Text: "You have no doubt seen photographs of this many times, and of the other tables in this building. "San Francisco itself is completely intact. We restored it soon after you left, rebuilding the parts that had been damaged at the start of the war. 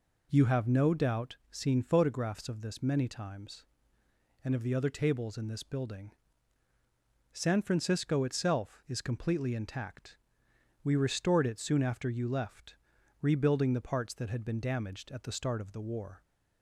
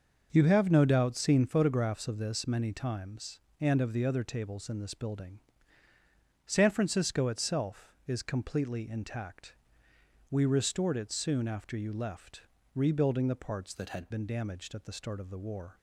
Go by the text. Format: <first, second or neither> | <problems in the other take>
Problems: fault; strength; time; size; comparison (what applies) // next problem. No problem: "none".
first | starts louder than the rest; until 1.3 s; 6.5 dB // changes voice from "that" to "had"; from 13.7 to 14.0 s; 0.3 s long